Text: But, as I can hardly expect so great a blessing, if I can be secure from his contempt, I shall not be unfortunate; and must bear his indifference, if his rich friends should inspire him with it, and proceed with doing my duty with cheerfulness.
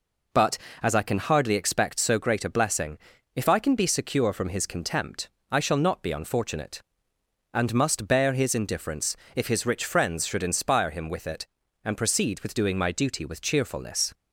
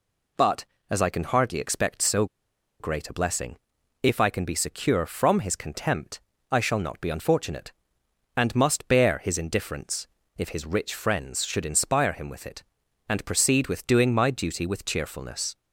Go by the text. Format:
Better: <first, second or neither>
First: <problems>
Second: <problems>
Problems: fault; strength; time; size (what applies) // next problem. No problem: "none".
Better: first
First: none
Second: pauses between "so" and "great"; noticeable; at 2.2 s; 0.55 s long